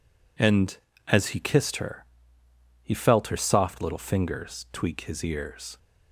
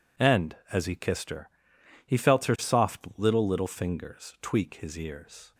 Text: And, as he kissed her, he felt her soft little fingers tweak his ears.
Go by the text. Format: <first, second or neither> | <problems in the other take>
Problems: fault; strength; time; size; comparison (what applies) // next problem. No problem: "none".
first | says "little" twice; at 3.4 s